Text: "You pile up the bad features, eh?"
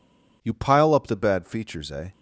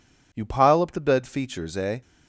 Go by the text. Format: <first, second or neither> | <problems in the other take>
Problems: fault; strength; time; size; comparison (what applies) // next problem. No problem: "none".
first | says "bed" for "bad"; at 1.0 s